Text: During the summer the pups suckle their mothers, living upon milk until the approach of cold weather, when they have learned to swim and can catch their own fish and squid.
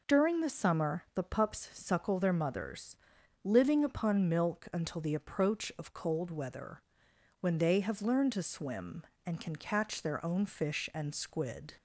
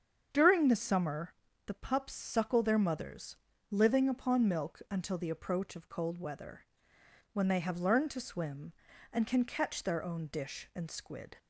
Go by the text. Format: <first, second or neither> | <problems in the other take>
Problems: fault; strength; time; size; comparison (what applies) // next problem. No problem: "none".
first | starts louder than the rest; strong; until 1.3 s; 7.5 dB // pauses between "summer" and "the"; slight; at 1.3 s; 0.32 s long // says "dish" for "fish"; at 10.2 s